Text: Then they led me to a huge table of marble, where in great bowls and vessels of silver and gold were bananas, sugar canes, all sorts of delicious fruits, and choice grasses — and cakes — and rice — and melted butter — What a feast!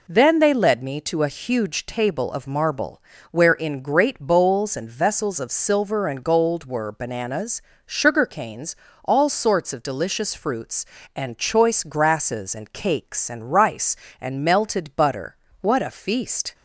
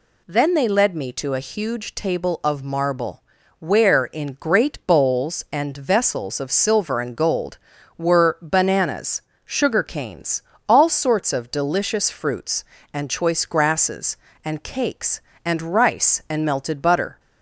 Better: first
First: none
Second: stops before "What a feast"; at 17.1 s

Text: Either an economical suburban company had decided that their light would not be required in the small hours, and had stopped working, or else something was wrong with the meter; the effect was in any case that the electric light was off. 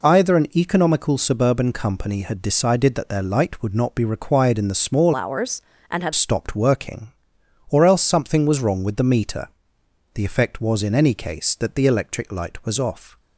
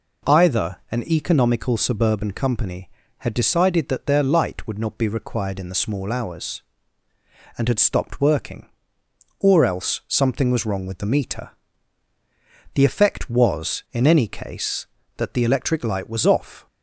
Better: second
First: changes voice from "hours" to "had"; from 5.1 to 6.1 s; 1.0 s long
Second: none

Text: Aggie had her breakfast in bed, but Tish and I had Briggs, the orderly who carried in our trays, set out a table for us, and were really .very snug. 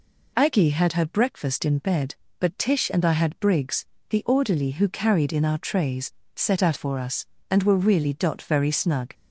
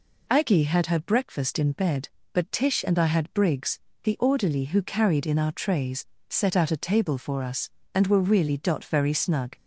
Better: second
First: skips "a table"; at 6.7 s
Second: none

